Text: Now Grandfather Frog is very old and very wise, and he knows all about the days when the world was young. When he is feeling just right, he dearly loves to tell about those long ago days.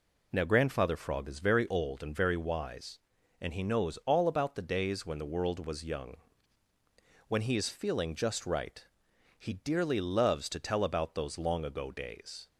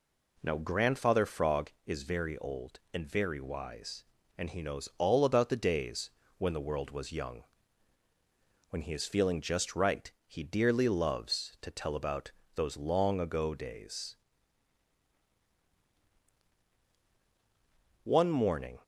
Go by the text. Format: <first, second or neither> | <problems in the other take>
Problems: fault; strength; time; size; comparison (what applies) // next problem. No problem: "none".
first | pauses between "days" and "when"; slight; at 6.0 s; 0.28 s long // pauses between "about" and "those"; slight; at 12.3 s; 0.24 s long // goes on to say "One morning"; noticeable; from 18.0 s on; 0.76 s long